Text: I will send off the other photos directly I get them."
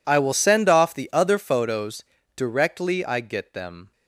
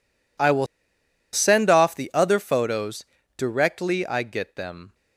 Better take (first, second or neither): first